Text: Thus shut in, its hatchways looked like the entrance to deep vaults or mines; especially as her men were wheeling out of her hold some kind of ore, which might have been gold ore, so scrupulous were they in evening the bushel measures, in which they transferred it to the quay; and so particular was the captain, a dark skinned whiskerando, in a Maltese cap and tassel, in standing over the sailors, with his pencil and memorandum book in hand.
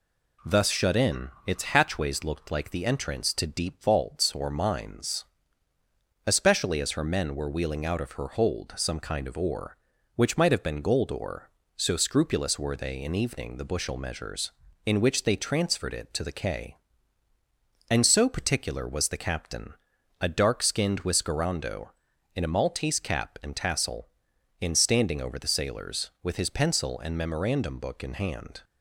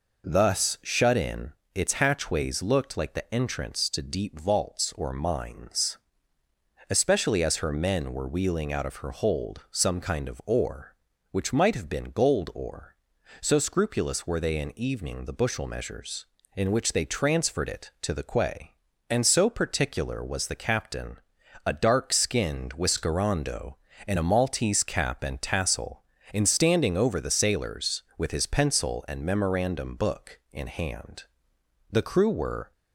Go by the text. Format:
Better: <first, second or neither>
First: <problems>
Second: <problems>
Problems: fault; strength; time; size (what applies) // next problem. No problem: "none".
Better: first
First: none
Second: goes on to say "The crew were"; noticeable; from 31.8 s on; 0.82 s long